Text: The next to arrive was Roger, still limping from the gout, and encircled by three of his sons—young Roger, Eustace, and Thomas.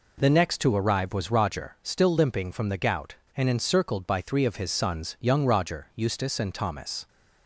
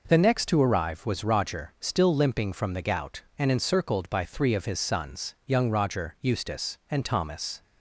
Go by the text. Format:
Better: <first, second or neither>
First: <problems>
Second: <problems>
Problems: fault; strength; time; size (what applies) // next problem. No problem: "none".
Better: neither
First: none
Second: none